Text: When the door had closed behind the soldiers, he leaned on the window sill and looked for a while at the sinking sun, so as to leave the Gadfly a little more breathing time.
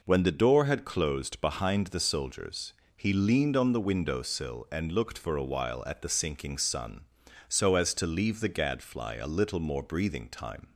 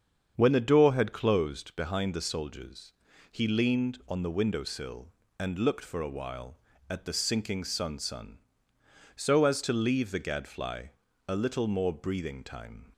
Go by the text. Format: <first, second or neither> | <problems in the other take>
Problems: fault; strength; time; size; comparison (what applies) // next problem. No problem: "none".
first | starts louder than the rest; strong; until 1.3 s; 7.5 dB // says "sun" twice; at 7.9 s // pauses between "Gadfly" and "a"; slight; at 10.9 s; 0.36 s long